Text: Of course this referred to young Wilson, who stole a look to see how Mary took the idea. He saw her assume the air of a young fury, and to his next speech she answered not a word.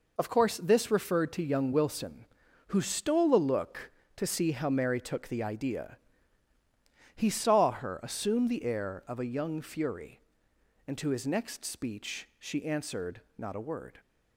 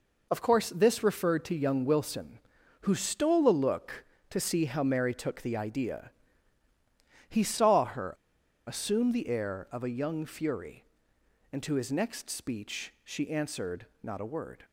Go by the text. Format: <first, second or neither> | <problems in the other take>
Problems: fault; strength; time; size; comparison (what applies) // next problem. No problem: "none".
first | pauses between "her" and "assume"; noticeable; at 8.1 s; 0.54 s long // pauses between "answered" and "not"; slight; at 13.8 s; 0.16 s long; slight in the first